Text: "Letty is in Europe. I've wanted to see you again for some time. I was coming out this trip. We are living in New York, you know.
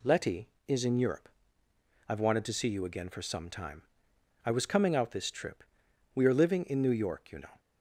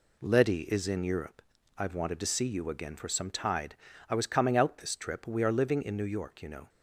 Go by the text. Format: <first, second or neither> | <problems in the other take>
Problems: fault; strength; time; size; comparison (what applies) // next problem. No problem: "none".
first | says "tide" for "time"; at 3.2 s